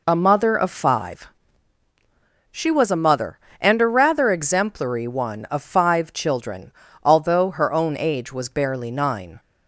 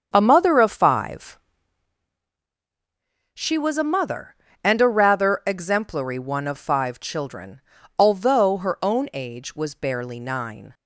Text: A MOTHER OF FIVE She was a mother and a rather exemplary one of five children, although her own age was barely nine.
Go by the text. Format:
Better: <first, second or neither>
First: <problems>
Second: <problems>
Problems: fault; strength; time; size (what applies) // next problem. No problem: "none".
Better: first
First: pauses between "FIVE" and "She"; at 1.2 s; 1.2 s long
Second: starts louder than the rest; strong; until 1.8 s; 7.5 dB // pauses between "FIVE" and "She"; strong; at 1.3 s; 1.9 s long